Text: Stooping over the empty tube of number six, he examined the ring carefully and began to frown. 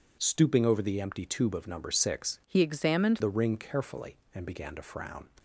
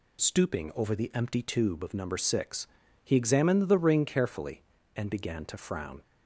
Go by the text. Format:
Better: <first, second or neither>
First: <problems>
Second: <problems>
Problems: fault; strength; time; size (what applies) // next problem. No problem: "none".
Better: second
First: changes voice from "he" to "examined"; from 2.4 to 3.1 s; 0.7 s long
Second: none